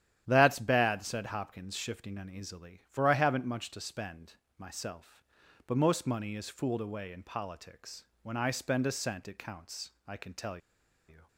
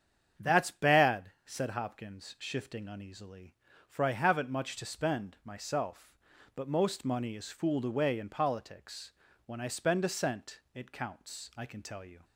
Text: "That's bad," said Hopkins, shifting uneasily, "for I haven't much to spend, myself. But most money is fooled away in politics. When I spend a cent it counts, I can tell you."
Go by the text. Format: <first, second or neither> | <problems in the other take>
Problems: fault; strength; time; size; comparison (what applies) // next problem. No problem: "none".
second | starts louder than the rest; strong; until 1.2 s; 11 dB; strong in the second // pauses between "tell" and "you"; noticeable; at 10.5 s; 0.51 s long